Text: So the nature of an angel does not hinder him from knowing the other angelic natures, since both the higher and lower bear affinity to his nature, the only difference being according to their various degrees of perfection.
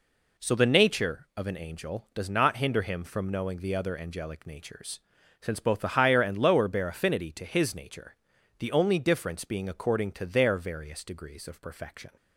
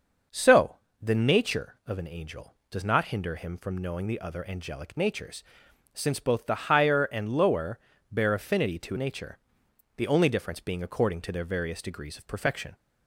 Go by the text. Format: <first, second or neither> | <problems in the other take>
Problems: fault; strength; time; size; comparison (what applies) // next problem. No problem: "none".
first | starts louder than the rest; until 1.5 s; 6.5 dB // pauses between "So" and "the"; slight; at 0.7 s; 0.24 s long // pauses between "lower" and "bear"; slight; at 7.7 s; 0.32 s long // skips "his"; at 8.9 s